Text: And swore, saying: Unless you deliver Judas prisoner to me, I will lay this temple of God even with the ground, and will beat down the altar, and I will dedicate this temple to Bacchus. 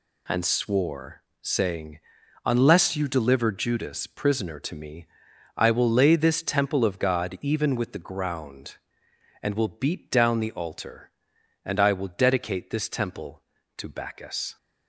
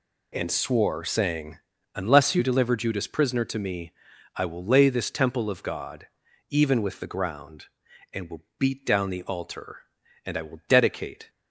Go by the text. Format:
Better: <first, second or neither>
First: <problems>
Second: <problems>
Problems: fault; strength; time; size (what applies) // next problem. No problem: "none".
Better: first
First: none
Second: pauses between "God" and "even"; at 6.0 s; 0.42 s long // pauses between "will" and "beat"; slight; at 8.4 s; 0.16 s long // stops before "this temple to Bacchus"; at 11.2 s